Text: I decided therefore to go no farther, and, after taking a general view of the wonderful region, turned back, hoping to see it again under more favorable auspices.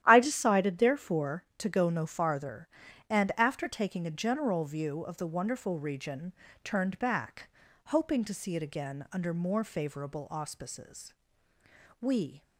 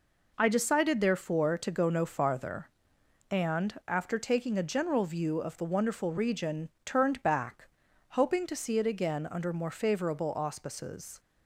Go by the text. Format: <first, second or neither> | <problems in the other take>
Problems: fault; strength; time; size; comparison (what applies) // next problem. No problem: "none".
second | starts louder than the rest; strong; until 1.0 s; 12 dB // goes on to say "We"; slight; from 11.9 s on; 0.42 s long